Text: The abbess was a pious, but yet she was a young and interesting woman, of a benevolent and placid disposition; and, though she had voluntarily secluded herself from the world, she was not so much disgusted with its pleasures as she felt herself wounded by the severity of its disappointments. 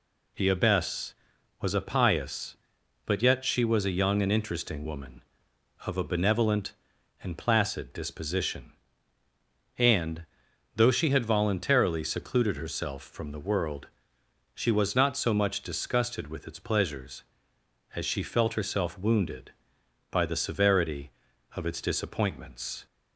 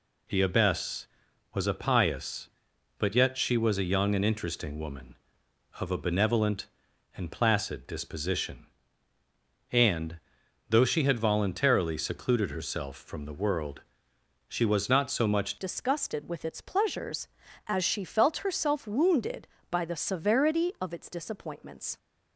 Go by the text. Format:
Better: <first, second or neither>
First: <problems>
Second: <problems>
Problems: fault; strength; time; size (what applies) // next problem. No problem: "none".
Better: first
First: none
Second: changes voice at "disgusted"; from 15.5 s on; 6.4 s long